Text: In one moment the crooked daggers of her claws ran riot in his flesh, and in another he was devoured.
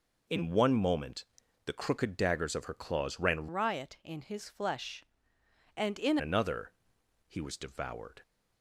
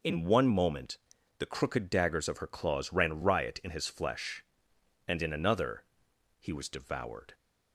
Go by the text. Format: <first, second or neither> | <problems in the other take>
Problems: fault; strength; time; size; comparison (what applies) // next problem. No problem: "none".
second | pauses between "moment" and "the"; at 1.2 s; 0.40 s long; also in the second // changes voice from "riot" to "in"; from 3.4 to 6.1 s; 2.7 s long // pauses between "another" and "he"; noticeable; at 6.7 s; 0.56 s long; noticeable in the second